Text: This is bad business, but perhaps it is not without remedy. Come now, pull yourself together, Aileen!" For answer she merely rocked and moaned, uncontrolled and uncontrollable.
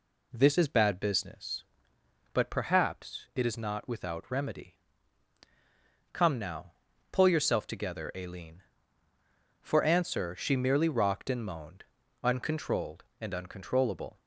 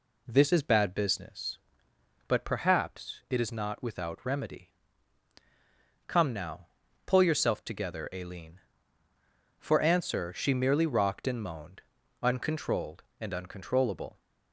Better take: neither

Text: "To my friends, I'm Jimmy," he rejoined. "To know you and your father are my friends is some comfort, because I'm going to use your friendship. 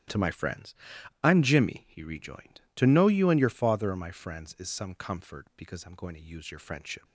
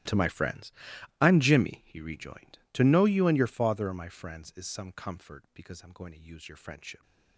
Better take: first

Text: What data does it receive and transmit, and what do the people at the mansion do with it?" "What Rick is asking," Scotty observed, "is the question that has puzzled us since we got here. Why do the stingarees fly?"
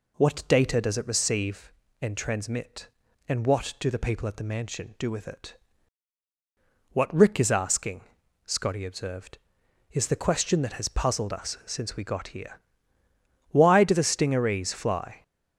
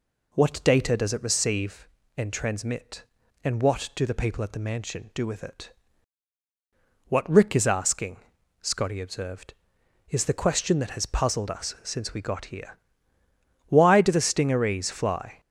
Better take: neither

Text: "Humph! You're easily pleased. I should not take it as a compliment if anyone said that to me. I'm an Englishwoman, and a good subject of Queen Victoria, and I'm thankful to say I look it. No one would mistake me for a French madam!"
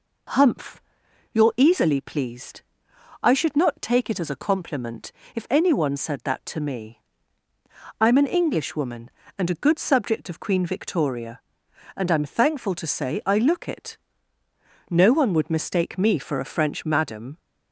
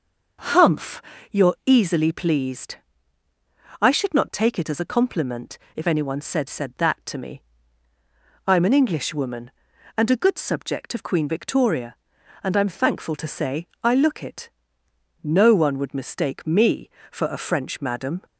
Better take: first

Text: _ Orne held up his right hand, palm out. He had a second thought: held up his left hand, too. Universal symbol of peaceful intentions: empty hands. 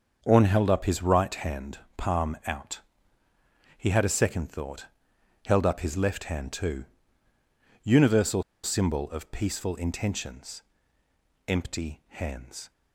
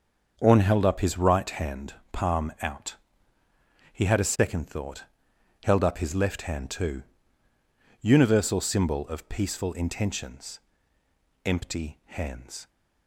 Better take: second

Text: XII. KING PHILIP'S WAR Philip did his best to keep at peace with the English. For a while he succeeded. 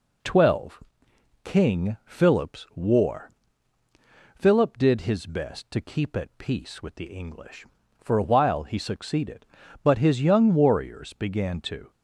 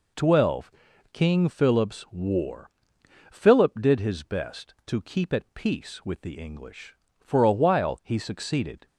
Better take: second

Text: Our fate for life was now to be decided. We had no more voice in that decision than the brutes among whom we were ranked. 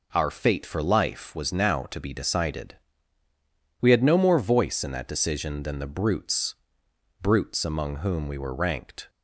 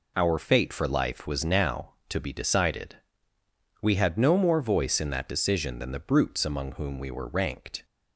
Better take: second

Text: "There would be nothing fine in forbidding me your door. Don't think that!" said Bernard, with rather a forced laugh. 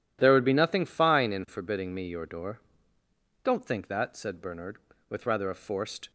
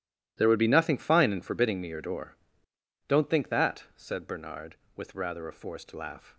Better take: second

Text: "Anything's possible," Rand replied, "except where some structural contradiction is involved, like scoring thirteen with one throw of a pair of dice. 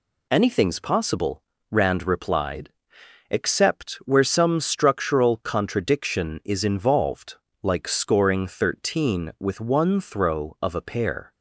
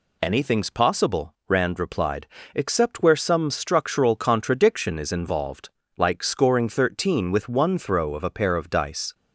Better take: second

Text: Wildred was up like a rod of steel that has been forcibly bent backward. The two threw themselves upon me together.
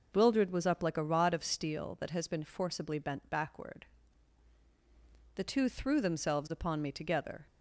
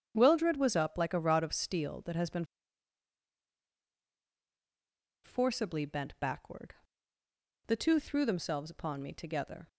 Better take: first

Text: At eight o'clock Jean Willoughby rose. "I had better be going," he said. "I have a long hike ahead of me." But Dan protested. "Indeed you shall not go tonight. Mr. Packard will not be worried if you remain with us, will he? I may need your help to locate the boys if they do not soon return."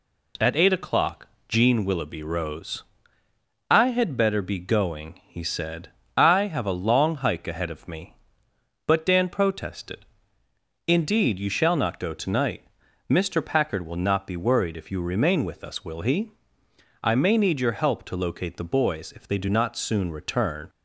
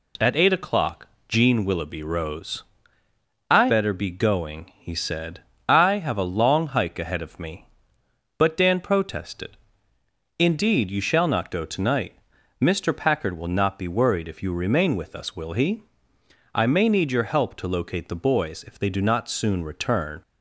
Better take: first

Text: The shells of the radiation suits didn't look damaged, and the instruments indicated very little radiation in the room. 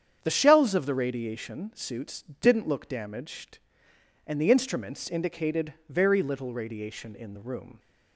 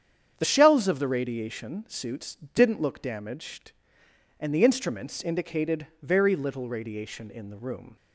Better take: neither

